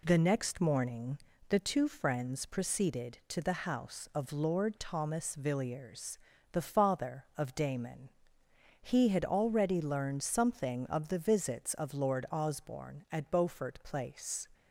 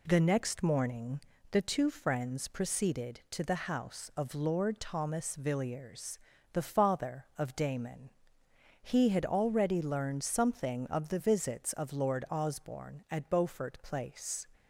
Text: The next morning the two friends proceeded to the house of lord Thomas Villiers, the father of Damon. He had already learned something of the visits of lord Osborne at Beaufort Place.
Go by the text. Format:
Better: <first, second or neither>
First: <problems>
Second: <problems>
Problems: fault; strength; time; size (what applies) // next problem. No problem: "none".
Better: neither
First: pauses between "morning" and "the"; slight; at 1.1 s; 0.32 s long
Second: pauses between "morning" and "the"; slight; at 1.1 s; 0.32 s long